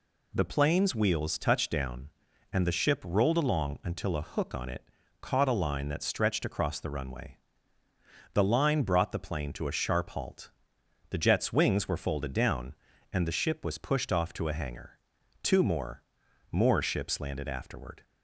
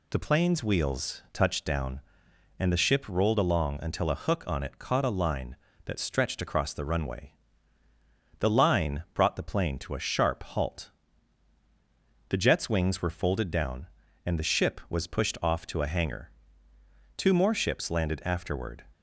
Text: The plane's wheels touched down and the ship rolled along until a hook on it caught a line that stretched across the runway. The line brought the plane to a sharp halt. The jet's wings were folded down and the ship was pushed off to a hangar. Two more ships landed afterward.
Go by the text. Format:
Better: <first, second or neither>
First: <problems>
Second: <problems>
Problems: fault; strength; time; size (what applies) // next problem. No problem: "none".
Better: second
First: pauses between "it" and "caught"; at 4.8 s; 0.38 s long // says "more" twice; at 16.5 s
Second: none